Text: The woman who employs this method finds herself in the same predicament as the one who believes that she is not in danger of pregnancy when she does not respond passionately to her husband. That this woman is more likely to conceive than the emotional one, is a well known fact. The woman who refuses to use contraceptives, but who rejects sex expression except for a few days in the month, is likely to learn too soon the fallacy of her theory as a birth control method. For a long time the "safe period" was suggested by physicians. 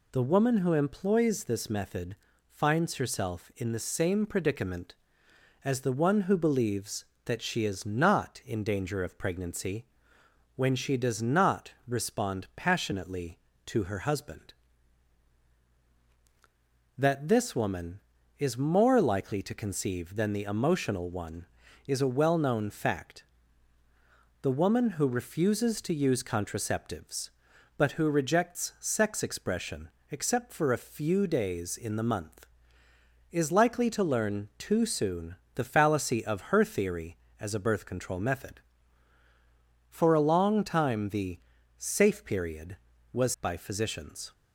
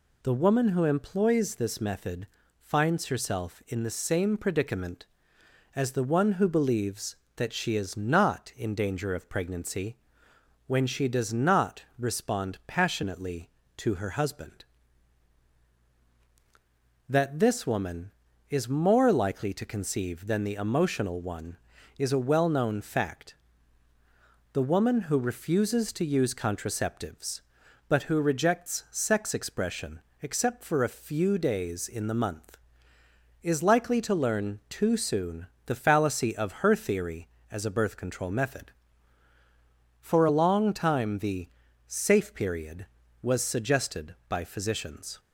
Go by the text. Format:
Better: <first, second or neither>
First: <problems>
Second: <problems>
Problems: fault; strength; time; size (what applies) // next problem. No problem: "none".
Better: second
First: pauses between "method" and "finds"; slight; at 2.1 s; 0.34 s long // pauses between "pregnancy" and "when"; noticeable; at 9.8 s; 0.72 s long // pauses between "expression" and "except"; slight; at 29.8 s; 0.20 s long // pauses between "soon" and "the"; slight; at 35.3 s; 0.20 s long // pauses between "the" and "safe"; at 41.3 s; 0.38 s long // skips "suggested"; at 43.3 s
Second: pauses between "method" and "finds"; slight; at 2.2 s; 0.34 s long // pauses between "pregnancy" and "when"; noticeable; at 9.9 s; 0.72 s long // pauses between "expression" and "except"; slight; at 30.0 s; 0.20 s long // pauses between "soon" and "the"; slight; at 35.4 s; 0.20 s long // pauses between "the" and "safe"; at 41.4 s; 0.38 s long